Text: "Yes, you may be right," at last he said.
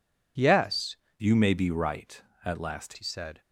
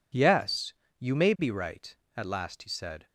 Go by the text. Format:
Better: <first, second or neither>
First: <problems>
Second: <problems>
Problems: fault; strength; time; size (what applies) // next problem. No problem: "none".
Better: second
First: changes voice from "you" to "last"; from 1.2 to 2.9 s; 1.7 s long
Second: none